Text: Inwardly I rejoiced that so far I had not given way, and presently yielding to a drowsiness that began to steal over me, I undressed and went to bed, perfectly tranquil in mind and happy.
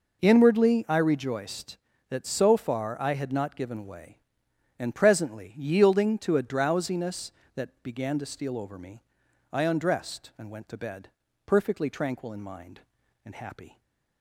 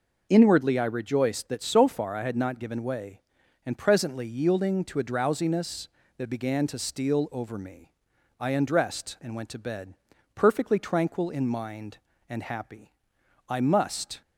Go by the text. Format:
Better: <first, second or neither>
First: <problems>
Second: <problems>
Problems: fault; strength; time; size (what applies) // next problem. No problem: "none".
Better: first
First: none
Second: goes on to say "I must"; noticeable; from 13.4 s on; 0.74 s long